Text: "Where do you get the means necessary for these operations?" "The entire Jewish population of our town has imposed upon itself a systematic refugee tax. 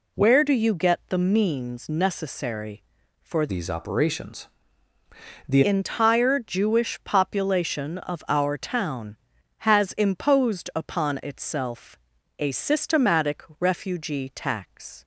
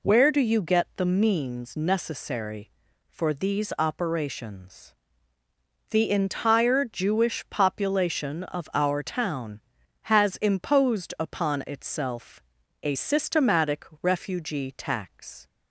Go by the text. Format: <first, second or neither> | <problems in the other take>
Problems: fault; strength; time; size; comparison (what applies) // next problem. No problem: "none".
second | changes voice from "these" to "The"; from 3.4 to 5.6 s; 2.2 s long // pauses between "itself" and "a"; at 11.9 s; 0.40 s long; also in the second